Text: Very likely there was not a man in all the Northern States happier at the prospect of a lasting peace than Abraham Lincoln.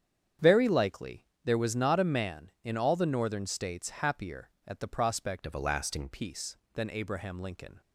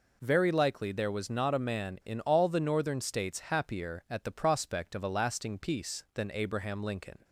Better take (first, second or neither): second